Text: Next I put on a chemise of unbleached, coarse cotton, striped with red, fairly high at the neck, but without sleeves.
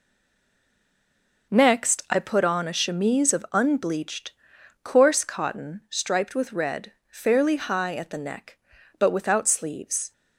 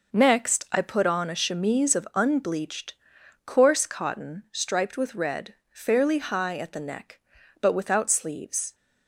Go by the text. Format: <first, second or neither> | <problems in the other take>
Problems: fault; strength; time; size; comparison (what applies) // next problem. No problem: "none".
second | stays silent before the first word; noticeable; until 1.5 s; 1.5 s long